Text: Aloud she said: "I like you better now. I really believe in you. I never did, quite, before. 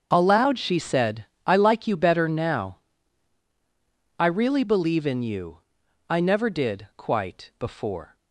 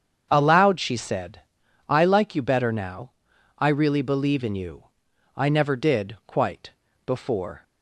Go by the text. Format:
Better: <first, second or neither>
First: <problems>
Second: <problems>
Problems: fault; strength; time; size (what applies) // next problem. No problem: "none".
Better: neither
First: starts louder than the rest; until 1.1 s; 7 dB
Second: starts louder than the rest; strong; until 1.3 s; 7.5 dB